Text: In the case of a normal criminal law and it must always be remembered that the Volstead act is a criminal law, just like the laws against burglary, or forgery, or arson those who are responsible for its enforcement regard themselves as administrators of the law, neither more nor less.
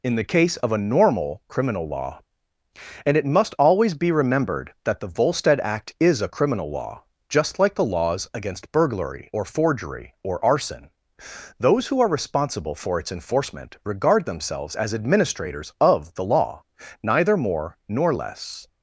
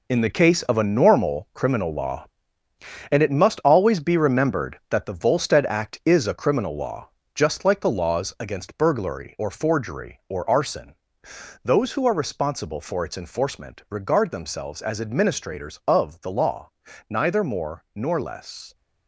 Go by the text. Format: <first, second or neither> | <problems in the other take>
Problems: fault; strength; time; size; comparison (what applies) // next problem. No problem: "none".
first | gets quieter; strong; throughout; 9 dB // pauses between "arson" and "those"; noticeable; at 10.9 s; 0.66 s long; noticeable in the first